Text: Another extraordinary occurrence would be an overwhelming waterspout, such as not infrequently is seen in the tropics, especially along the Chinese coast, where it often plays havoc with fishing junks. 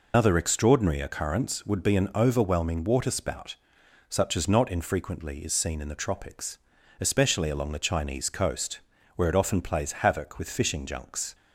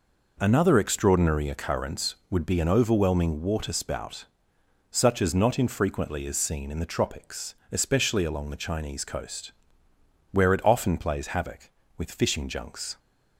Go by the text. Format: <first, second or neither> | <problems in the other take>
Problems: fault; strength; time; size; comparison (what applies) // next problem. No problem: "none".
second | loses the start of "Another"; at 0.1 s; 150 ms